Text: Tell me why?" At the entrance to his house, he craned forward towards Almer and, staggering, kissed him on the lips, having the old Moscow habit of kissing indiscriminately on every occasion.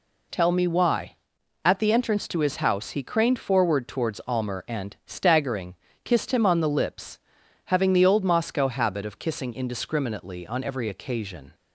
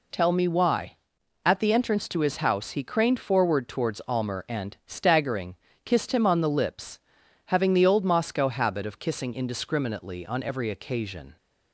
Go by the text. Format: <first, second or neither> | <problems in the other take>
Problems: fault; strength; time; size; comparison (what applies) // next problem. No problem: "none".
neither | none